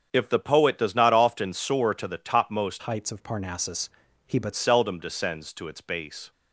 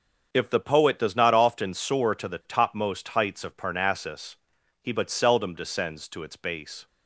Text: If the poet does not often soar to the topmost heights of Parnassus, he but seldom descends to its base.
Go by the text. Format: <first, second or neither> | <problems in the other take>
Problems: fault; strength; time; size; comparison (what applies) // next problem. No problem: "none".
second | starts louder than the rest; strong; until 1.1 s; 7.5 dB; also in the second // changes voice from "heights" to "but"; from 2.8 to 4.5 s; 1.7 s long